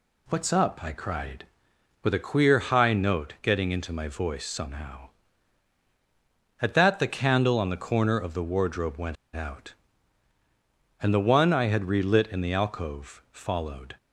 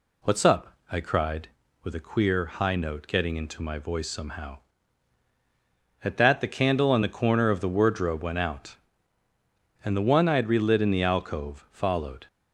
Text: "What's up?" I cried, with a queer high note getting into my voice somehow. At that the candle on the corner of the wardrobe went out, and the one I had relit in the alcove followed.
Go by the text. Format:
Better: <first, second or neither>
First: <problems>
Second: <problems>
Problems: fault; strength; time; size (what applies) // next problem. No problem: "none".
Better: second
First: pauses between "went" and "out"; slight; at 9.1 s; 0.18 s long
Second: none